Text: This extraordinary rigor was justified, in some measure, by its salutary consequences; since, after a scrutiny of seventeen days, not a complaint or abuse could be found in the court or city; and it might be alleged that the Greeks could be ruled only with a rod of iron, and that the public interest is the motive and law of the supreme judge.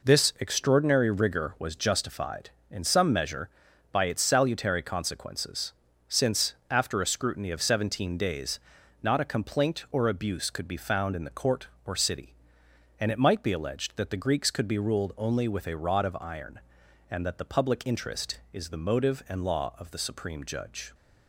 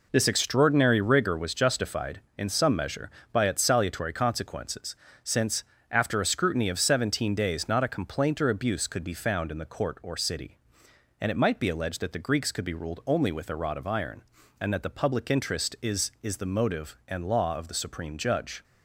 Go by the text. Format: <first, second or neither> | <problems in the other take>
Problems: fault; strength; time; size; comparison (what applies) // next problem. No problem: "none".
first | says "is" twice; at 16.2 s